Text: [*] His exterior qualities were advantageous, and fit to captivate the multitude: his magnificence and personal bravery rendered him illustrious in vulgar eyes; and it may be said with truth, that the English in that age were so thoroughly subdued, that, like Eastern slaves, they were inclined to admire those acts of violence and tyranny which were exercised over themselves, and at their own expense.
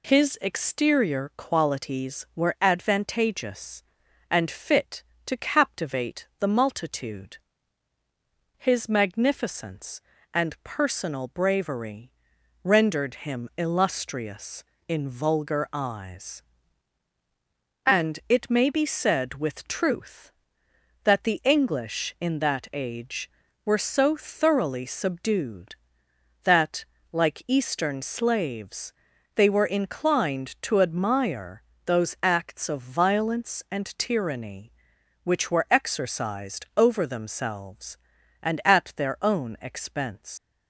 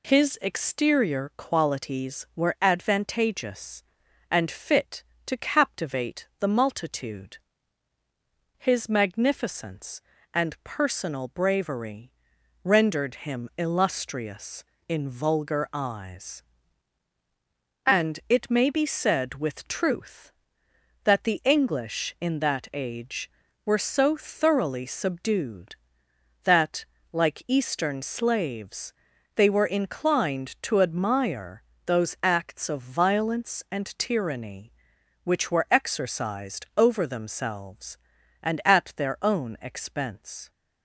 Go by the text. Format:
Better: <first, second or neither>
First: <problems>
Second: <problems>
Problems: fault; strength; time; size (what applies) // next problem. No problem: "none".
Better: second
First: pauses between "bravery" and "rendered"; noticeable; at 12.1 s; 0.50 s long // pauses between "admire" and "those"; slight; at 31.6 s; 0.22 s long // leaves "expense" unfinished; at 40.3 s; 115 ms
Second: pauses between "bravery" and "rendered"; noticeable; at 12.1 s; 0.50 s long // pauses between "admire" and "those"; slight; at 31.6 s; 0.22 s long